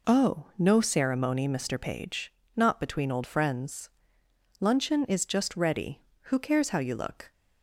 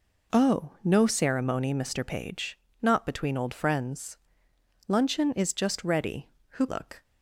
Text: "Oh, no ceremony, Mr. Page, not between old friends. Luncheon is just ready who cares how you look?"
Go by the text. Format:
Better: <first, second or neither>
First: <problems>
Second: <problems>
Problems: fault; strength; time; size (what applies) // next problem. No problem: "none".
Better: first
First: none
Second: skips "cares how you"; at 6.6 s